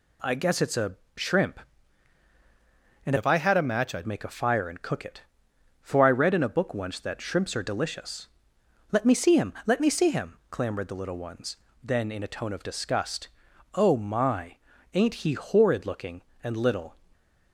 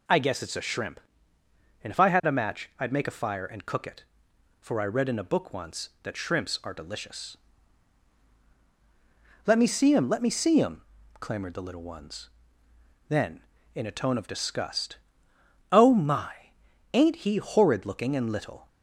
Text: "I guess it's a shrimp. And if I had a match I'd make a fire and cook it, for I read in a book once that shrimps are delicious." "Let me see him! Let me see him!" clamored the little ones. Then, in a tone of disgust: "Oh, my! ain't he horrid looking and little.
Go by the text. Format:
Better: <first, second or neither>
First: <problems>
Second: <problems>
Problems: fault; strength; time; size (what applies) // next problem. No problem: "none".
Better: second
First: pauses between "a" and "shrimp"; slight; at 0.9 s; 0.20 s long // changes voice from "if" to "I'd"; from 3.1 to 4.0 s; 0.9 s long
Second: none